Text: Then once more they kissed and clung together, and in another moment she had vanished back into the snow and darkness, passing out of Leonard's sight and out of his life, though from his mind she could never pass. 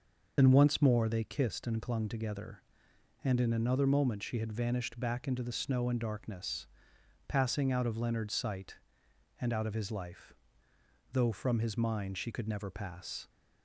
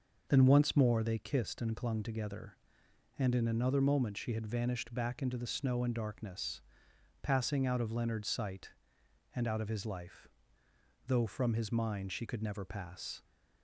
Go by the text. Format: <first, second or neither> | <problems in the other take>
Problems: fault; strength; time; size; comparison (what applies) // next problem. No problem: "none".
second | loses the start of "Then"; at 0.3 s; 35 ms